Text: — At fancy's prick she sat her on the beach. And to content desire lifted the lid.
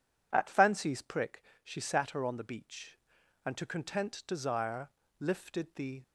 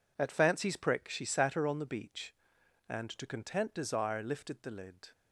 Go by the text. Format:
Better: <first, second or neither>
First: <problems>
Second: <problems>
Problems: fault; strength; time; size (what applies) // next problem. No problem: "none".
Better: second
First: pauses between "prick" and "she"; slight; at 1.4 s; 0.22 s long // pauses between "desire" and "lifted"; slight; at 4.9 s; 0.28 s long // stops before "lid"; at 6.0 s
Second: none